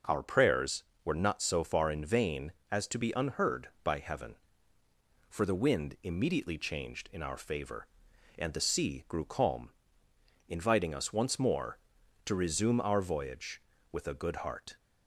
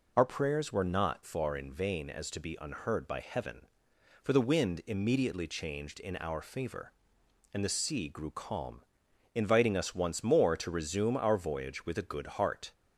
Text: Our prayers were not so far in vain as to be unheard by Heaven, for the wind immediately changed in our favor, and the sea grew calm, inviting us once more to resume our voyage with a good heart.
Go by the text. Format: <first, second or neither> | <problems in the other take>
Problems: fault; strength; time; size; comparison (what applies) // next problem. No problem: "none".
first | skips "so"; at 1.2 s